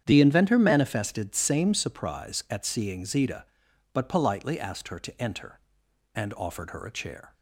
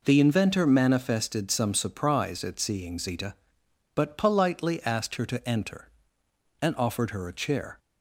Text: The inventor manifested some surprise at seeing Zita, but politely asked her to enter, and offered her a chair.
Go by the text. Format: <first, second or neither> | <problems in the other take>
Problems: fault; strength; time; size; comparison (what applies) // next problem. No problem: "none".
second | starts louder than the rest; strong; until 1.0 s; 9 dB // says "same" for "some"; at 1.3 s